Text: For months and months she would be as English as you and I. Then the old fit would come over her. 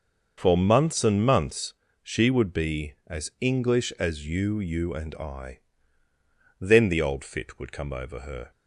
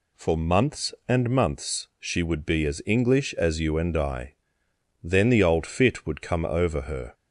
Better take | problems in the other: second | starts louder than the rest; noticeable; until 1.3 s; 6 dB // pauses between "months" and "she"; slight; at 1.7 s; 0.28 s long // says "you" twice; at 4.6 s

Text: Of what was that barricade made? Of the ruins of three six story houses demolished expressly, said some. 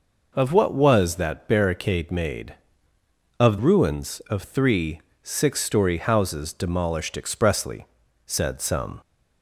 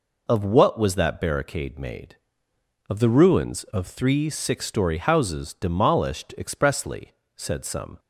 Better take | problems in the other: second | skips "the"; at 3.5 s // pauses between "three" and "six"; slight; at 4.9 s; 0.24 s long

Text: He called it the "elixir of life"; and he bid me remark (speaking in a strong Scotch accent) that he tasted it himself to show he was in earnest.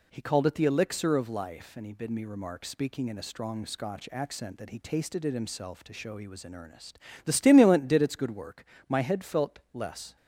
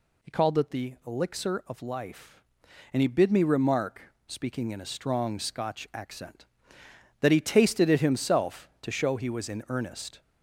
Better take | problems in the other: second | goes on to say "The stimulant did its good work My head felt less"; strong; from 7.2 s on; 2.9 s long

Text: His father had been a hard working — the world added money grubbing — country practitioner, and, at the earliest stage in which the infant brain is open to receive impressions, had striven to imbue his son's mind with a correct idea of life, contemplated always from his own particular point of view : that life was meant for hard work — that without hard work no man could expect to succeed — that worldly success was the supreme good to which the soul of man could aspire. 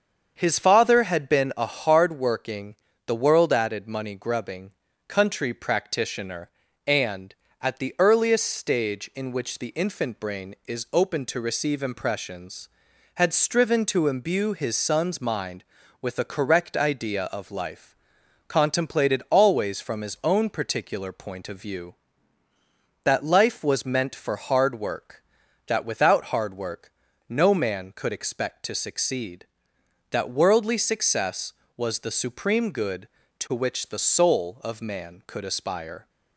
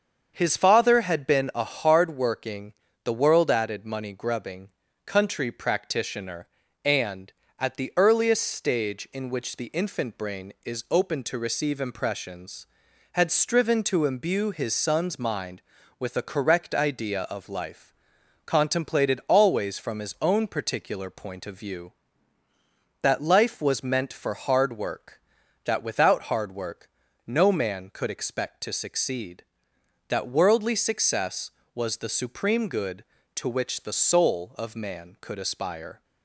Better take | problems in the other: neither | starts louder than the rest; the same in both // pauses between "work" and "no"; slight; the same in both

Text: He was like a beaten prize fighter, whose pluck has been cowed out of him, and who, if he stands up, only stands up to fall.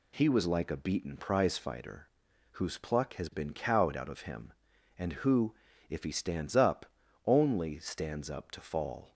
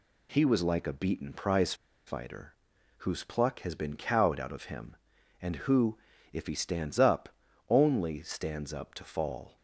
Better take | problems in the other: first | pauses between "prize" and "fighter"; slight; at 1.7 s; 0.32 s long

